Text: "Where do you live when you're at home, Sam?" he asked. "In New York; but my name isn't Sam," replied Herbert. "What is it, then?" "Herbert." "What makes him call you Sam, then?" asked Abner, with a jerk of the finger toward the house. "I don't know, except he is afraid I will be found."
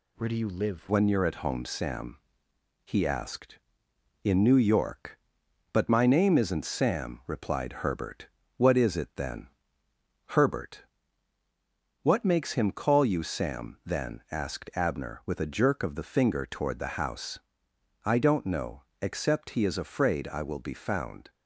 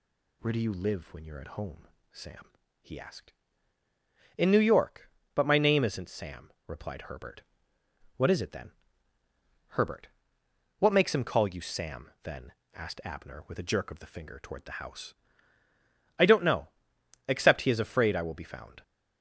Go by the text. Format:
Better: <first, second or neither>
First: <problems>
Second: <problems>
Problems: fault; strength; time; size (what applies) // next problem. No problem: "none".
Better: second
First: changes voice at "when"; from 0.8 s on; 20.4 s long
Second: none